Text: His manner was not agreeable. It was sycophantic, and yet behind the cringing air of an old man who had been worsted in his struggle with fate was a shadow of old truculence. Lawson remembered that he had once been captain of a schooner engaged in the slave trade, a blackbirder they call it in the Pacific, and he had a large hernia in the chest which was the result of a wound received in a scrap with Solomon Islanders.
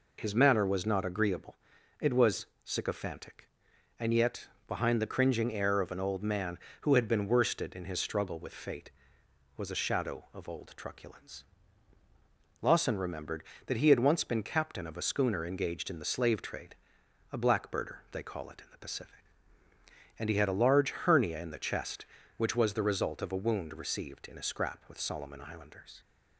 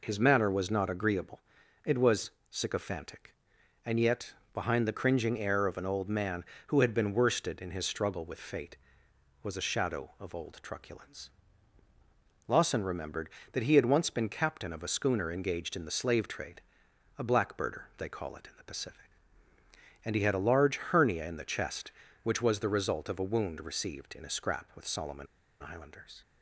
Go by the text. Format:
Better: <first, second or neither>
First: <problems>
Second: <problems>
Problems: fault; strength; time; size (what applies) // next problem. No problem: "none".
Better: first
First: pauses between "was" and "sycophantic"; slight; at 2.4 s; 0.18 s long // pauses between "yet" and "behind"; slight; at 4.4 s; 0.18 s long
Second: pauses between "was" and "sycophantic"; slight; at 2.2 s; 0.20 s long // pauses between "yet" and "behind"; slight; at 4.3 s; 0.18 s long // pauses between "Solomon" and "Islanders"; slight; at 25.2 s; 0.35 s long